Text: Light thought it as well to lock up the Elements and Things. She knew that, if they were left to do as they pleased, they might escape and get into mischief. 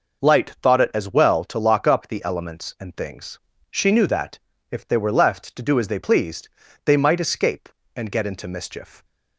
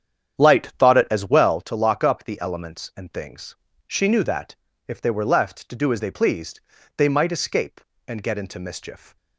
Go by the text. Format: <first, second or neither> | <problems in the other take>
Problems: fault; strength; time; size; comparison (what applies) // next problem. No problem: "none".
first | starts louder than the rest; strong; until 1.6 s; 9 dB